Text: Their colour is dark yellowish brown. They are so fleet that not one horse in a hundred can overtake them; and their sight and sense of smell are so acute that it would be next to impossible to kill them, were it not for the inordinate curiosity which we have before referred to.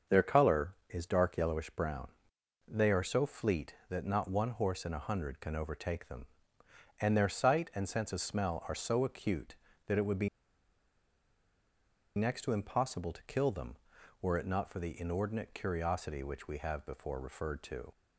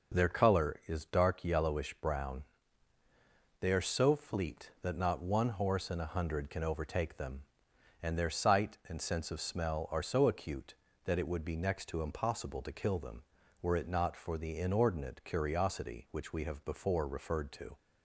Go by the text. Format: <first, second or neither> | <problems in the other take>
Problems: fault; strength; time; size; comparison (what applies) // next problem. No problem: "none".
second | starts louder than the rest; until 1.2 s; 6.5 dB // pauses between "be" and "next"; strong; at 10.2 s; 1.8 s long